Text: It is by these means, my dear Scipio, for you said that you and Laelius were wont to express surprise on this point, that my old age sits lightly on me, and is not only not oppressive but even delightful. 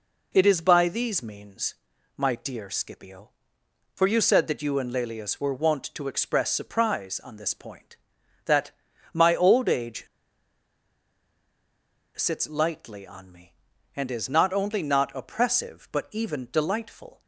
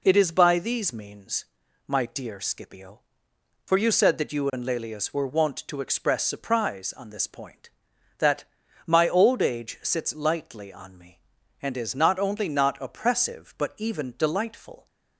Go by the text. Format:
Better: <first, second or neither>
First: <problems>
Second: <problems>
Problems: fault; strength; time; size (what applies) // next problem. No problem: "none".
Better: second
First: pauses between "that" and "my"; at 8.6 s; 0.42 s long // pauses between "age" and "sits"; strong; at 10.0 s; 2.0 s long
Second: pauses between "that" and "my"; at 8.4 s; 0.42 s long